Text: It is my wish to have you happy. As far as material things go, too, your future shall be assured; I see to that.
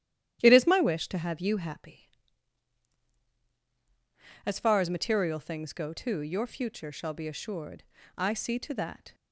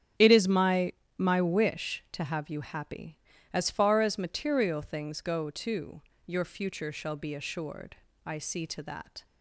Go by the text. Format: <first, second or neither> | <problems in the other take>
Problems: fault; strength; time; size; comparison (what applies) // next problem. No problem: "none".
first | starts louder than the rest; strong; until 1.4 s; 10 dB; strong in the first // says "my" twice; at 1.1 s